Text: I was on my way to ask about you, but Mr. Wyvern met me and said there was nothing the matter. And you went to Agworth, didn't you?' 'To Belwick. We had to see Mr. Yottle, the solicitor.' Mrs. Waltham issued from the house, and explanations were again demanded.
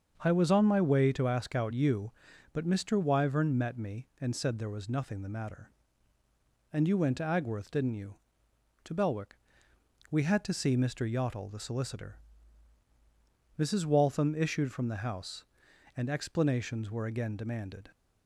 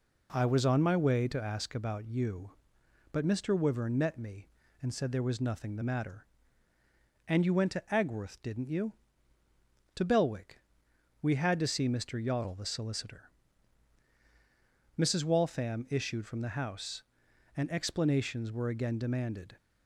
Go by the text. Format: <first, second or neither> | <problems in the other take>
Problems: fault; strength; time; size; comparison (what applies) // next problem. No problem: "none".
second | starts louder than the rest; until 1.2 s; 6.5 dB // says "out" for "about"; at 1.5 s